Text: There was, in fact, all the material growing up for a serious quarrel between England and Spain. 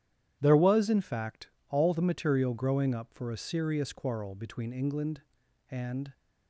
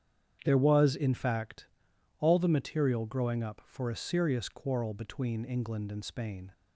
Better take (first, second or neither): second